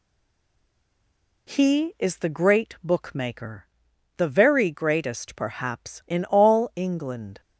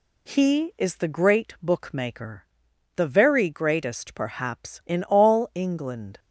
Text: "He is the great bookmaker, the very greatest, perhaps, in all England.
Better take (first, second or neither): second